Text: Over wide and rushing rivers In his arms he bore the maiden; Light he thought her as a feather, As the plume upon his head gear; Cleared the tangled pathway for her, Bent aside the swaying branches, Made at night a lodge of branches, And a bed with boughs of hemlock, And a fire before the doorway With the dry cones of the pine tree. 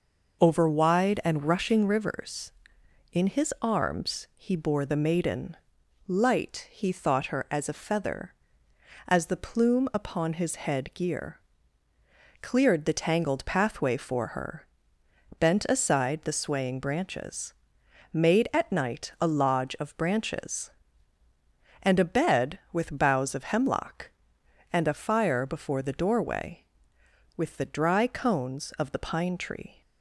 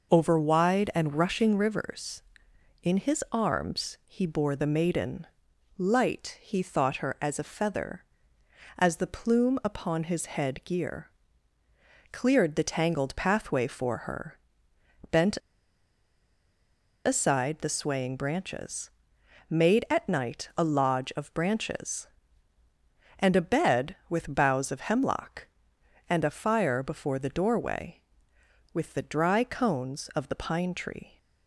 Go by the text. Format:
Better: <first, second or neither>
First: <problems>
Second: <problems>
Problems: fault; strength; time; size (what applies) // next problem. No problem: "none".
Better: first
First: none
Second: pauses between "Bent" and "aside"; strong; at 15.3 s; 1.6 s long